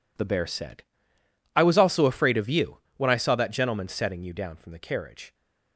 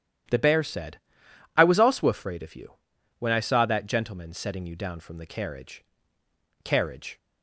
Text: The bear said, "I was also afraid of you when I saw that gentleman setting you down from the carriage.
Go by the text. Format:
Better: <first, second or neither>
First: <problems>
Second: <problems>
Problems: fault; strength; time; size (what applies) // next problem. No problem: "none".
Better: first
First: pauses between "you" and "when"; slight; at 2.7 s; 0.18 s long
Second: starts louder than the rest; strong; until 1.8 s; 11 dB // pauses between "you" and "when"; noticeable; at 2.7 s; 0.46 s long // says "carriage" twice; at 6.6 s